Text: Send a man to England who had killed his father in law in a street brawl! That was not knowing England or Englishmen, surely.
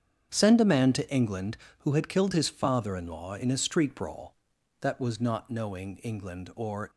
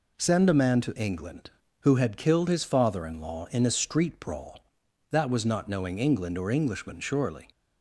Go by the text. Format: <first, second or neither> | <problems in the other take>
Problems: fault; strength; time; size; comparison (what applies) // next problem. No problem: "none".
second | starts louder than the rest; strong; until 1.3 s; 8 dB // stops before "Englishmen surely"; at 6.9 s